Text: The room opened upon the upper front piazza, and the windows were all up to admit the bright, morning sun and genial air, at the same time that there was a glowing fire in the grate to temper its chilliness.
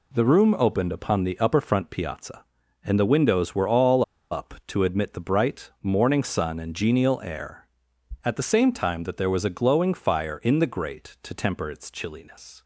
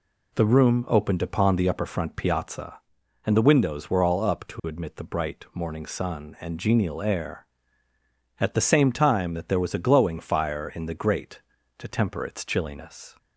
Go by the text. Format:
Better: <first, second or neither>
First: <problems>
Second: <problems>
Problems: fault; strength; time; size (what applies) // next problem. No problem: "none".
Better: second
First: pauses between "all" and "up"; slight; at 4.0 s; 0.27 s long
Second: none